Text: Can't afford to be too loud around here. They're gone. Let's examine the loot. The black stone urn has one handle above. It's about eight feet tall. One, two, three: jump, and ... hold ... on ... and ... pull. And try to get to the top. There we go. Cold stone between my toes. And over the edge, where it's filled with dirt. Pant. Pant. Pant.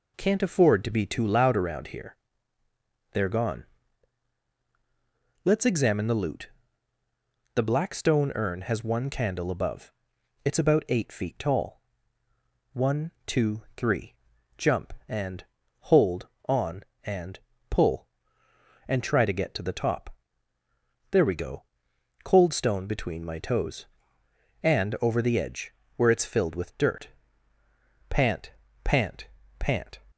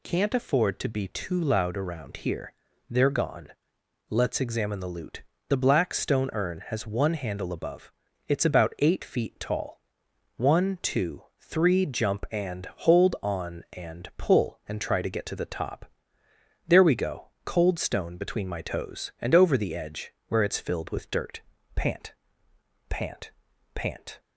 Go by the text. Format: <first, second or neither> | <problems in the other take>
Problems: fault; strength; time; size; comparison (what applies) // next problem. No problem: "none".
second | says "candle" for "handle"; at 9.1 s